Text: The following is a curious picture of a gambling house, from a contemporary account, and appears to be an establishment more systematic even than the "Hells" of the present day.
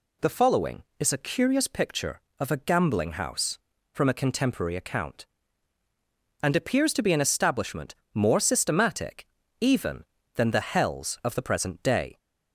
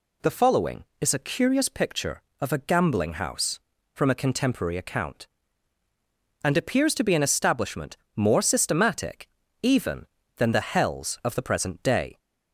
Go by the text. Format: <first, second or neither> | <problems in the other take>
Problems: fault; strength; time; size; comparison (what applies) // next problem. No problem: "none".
neither | pauses between "establishment" and "more"; slight; the same in both // pauses between "systematic" and "even"; slight; the same in both